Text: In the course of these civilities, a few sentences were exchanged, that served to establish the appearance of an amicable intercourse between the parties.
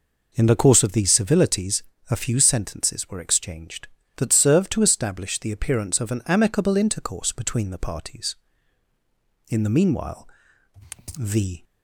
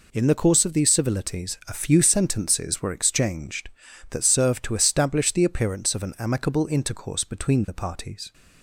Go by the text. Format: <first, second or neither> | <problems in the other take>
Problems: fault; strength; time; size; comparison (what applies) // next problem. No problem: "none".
second | goes on to say "In the meanwhile the"; strong; from 9.4 s on; 2.1 s long